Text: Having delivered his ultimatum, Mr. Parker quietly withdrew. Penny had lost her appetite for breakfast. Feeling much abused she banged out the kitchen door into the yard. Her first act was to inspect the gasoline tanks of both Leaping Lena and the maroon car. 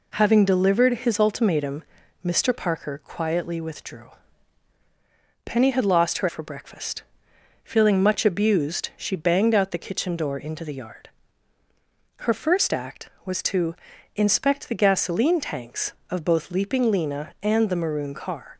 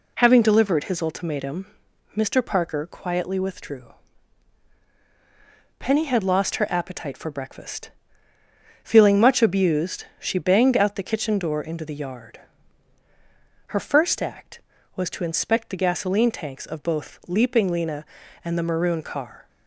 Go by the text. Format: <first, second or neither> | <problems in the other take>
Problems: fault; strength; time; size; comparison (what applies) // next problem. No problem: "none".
second | skips "appetite"; at 6.2 s // pauses between "to" and "inspect"; at 13.7 s; 0.44 s long